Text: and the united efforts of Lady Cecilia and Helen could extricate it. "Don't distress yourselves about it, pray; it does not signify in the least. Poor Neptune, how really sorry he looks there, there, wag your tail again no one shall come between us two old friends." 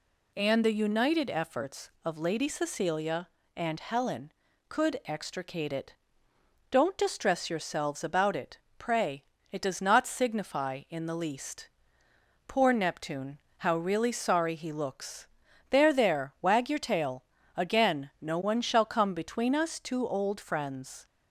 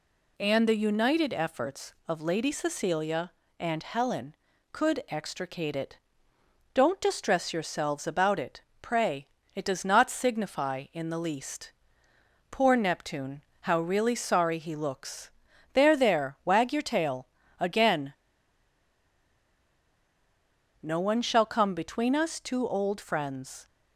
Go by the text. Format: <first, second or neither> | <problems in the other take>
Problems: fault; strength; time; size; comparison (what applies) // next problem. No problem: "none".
first | pauses between "looks" and "there"; at 15.3 s; 0.42 s long; also in the first // pauses between "tail" and "again"; slight; at 17.2 s; 0.34 s long; slight in the first // pauses between "again" and "no"; strong; at 18.1 s; 2.7 s long